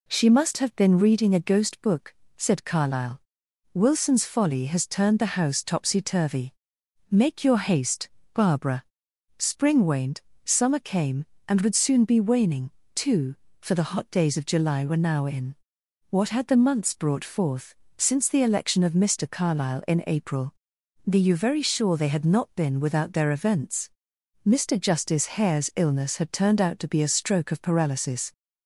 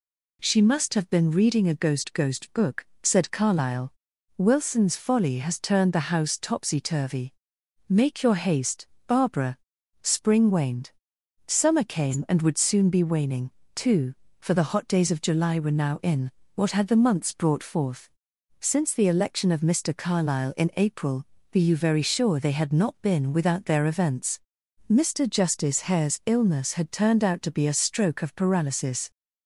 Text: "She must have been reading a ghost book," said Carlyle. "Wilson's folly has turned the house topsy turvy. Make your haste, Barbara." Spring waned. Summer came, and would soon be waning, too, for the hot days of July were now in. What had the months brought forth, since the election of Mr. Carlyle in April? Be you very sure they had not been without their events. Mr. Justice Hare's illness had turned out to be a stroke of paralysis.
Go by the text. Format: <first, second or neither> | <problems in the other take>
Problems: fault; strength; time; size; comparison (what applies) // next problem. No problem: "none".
first | says "ghost" twice; at 2.1 s